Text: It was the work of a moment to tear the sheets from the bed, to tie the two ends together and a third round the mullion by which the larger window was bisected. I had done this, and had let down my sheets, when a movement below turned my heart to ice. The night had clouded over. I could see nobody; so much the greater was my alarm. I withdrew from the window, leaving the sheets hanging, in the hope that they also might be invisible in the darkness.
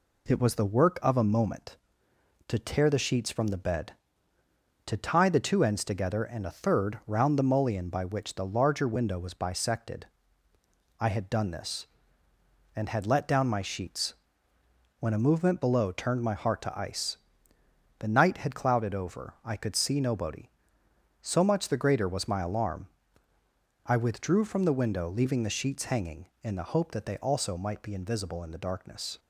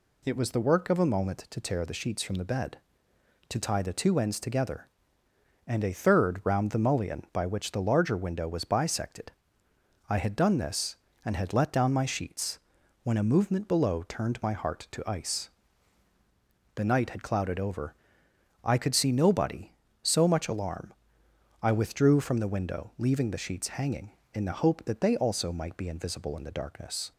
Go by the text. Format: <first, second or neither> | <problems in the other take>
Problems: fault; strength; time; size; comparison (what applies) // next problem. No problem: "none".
first | skips "the greater was my"; at 20.4 s